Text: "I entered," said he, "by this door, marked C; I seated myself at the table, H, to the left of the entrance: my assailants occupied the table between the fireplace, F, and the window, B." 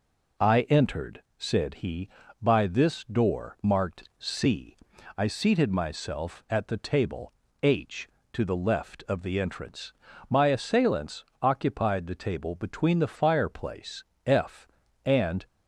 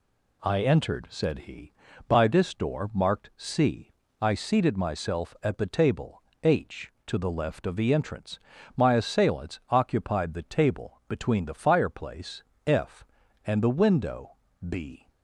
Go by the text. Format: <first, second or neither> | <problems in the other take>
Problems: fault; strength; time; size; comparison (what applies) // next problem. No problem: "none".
second | pauses between "assailants" and "occupied"; slight; at 11.2 s; 0.16 s long // stops before "the window B"; at 15.4 s